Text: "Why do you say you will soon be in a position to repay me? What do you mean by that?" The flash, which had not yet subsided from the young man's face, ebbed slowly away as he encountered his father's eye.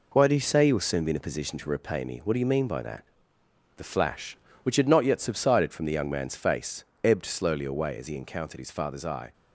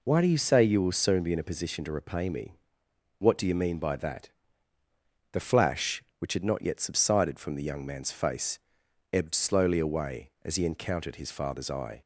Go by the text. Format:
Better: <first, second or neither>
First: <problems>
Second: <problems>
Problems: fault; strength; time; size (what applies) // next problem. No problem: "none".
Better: second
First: gets quieter; noticeable; throughout; 6 dB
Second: none